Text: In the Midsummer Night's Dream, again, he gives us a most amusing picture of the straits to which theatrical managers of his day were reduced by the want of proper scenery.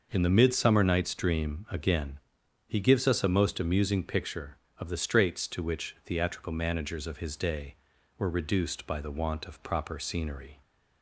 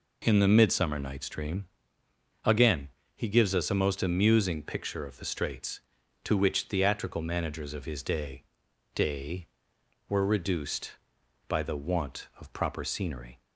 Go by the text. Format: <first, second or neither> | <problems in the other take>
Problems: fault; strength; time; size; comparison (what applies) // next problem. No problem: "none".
first | says "day" twice; at 8.9 s